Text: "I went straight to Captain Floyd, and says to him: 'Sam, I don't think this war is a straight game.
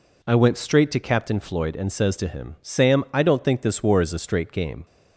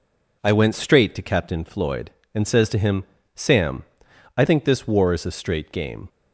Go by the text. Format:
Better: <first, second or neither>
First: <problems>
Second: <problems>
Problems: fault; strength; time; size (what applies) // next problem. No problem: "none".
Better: first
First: none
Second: skips "don't"; at 4.4 s